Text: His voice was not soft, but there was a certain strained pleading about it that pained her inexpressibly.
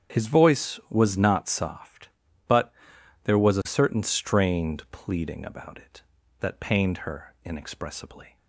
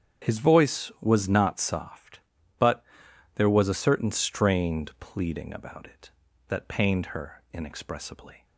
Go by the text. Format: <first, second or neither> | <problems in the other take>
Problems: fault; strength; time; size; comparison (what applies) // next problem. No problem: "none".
neither | starts louder than the rest; strong; the same in both // pauses between "but" and "there"; noticeable; the same in both